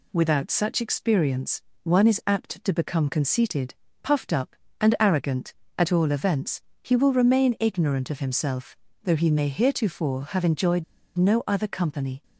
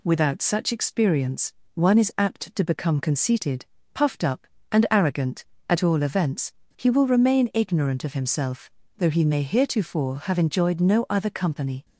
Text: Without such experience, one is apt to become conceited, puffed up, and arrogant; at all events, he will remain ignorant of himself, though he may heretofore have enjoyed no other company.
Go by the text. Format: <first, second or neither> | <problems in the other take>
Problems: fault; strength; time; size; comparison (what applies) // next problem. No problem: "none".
second | pauses between "enjoyed" and "no"; slight; at 10.8 s; 0.34 s long